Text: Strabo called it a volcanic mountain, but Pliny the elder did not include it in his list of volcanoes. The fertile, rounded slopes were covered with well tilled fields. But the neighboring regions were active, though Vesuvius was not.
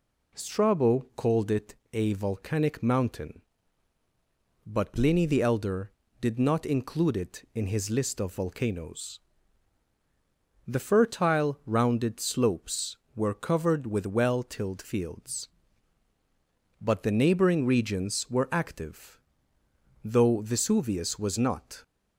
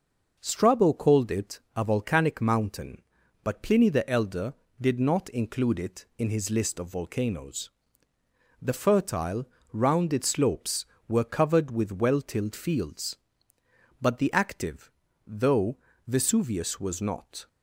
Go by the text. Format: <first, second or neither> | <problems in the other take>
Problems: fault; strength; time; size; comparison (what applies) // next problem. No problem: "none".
first | pauses between "it" and "a"; slight; at 1.5 s; 0.16 s long; slight in the first // skips "neighboring regions were"; at 14.3 s // pauses between "though" and "Vesuvius"; slight; at 15.7 s; 0.28 s long